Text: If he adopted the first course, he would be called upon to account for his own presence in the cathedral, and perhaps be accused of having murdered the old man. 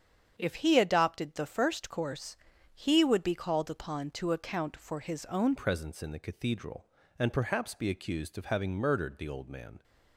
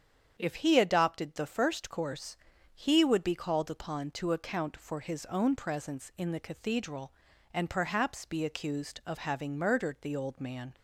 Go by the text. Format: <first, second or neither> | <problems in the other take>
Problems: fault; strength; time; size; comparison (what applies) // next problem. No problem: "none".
second | starts louder than the rest; strong; until 1.3 s; 7.5 dB; strong in the second // changes voice at "presence"; from 5.5 s on; 4.3 s long